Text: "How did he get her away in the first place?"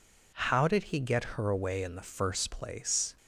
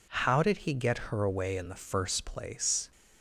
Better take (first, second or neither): neither